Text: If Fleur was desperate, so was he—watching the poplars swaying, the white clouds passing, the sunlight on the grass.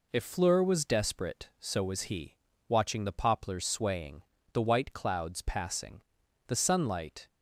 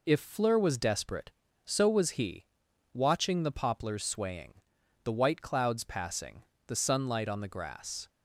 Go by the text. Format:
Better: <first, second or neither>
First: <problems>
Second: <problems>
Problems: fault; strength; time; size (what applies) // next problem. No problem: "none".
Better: second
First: stops before "on the grass"; at 7.2 s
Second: none